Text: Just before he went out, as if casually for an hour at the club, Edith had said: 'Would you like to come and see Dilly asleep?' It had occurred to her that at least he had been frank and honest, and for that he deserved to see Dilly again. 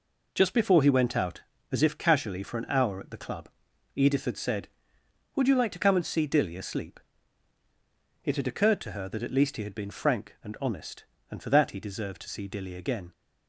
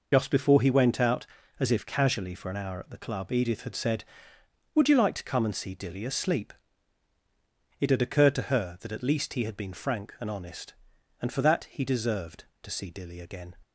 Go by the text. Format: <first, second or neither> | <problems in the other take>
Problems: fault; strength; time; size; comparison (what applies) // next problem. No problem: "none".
first | loses the start of "Just"; at 0.1 s; 55 ms